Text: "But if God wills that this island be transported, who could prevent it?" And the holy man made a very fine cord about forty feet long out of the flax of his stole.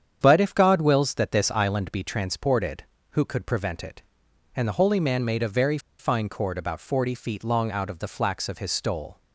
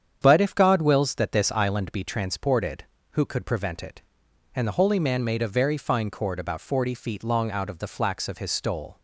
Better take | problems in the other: second | starts louder than the rest; strong; until 1.2 s; 8.5 dB; strong in the second // pauses between "very" and "fine"; slight; at 5.7 s; 0.21 s long

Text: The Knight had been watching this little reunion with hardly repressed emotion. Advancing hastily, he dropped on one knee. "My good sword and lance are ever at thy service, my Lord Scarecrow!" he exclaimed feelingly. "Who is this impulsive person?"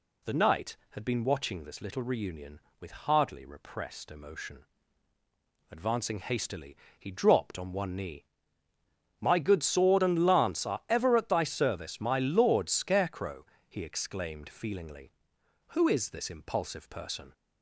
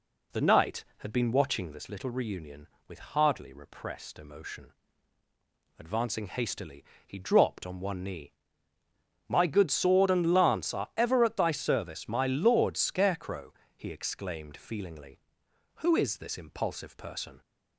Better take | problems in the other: first | starts louder than the rest; slight; until 2.0 s; 3 dB

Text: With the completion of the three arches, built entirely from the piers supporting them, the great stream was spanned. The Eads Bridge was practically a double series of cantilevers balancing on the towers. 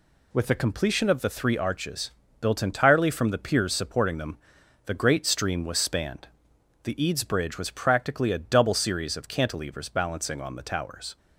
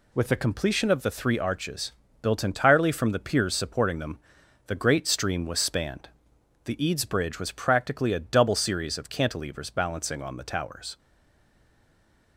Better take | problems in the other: first | stays silent after the last word; noticeable; from 10.9 s on; 1.4 s long

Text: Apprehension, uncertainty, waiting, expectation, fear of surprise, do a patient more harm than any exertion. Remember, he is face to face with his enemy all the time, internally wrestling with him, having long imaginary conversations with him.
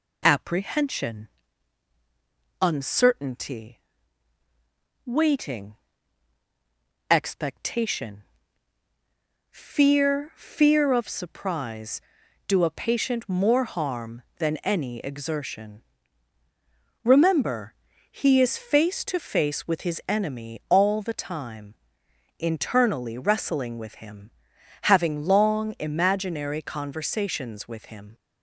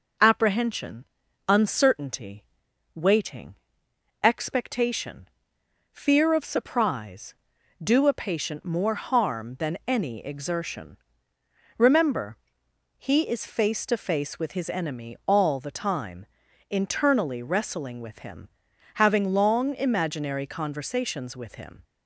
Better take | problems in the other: second | says "fear" twice; at 10.3 s

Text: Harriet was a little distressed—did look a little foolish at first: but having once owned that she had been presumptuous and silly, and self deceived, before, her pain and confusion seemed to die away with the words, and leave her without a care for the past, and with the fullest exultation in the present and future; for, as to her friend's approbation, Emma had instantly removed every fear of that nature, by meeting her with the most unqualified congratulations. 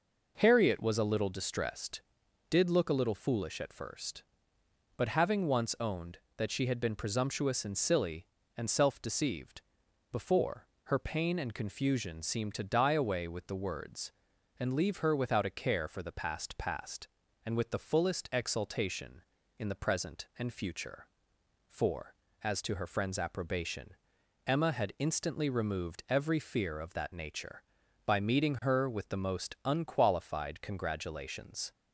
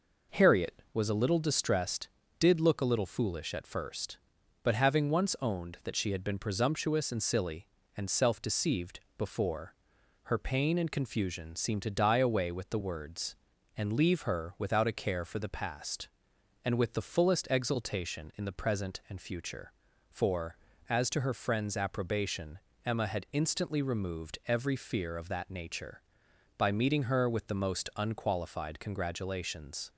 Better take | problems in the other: second | says "past" twice; at 16.5 s

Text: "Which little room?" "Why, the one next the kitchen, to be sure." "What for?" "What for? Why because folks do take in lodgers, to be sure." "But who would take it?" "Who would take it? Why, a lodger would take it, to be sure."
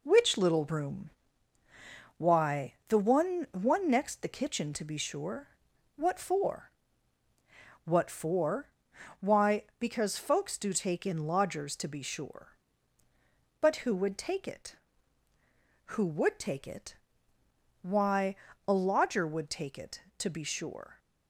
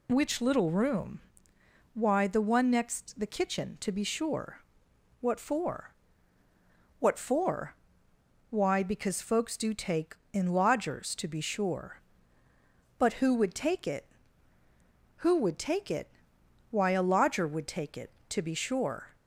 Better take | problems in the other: second | says "one" twice; at 3.5 s

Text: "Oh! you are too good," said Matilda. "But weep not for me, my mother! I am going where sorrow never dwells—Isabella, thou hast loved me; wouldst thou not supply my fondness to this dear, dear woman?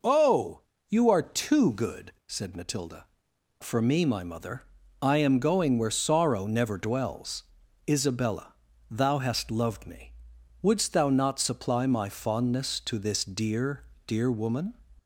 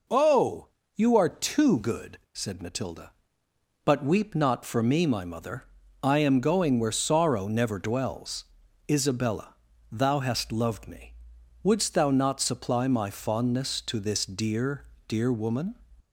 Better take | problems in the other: second | skips "But weep not"; at 3.3 s

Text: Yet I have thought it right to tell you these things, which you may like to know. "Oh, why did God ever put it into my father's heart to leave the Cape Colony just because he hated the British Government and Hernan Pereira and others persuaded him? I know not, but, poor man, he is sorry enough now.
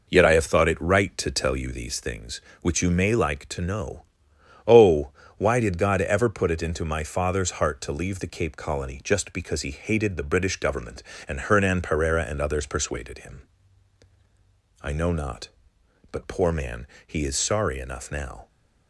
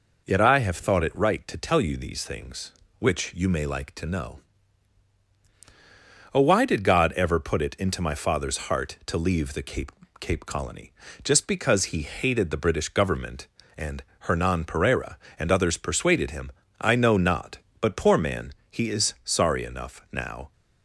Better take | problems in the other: first | says "Cape" twice; at 10.2 s // pauses between "Colony" and "just"; slight; at 10.9 s; 0.30 s long // pauses between "and" and "Hernan"; slight; at 14.0 s; 0.16 s long

